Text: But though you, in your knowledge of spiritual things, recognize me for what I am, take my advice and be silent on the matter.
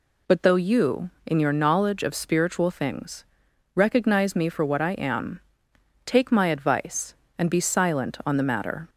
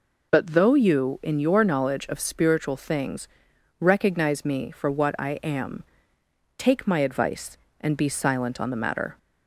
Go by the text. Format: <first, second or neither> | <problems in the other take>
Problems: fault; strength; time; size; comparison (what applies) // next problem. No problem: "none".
neither | none